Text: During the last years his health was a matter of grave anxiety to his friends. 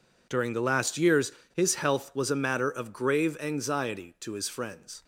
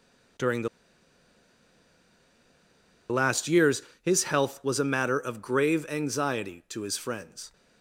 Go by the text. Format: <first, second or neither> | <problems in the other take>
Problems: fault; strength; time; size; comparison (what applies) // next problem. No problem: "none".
first | pauses between "the" and "last"; strong; at 0.6 s; 2.4 s long // pauses between "years" and "his"; slight; at 3.8 s; 0.20 s long; slight in the first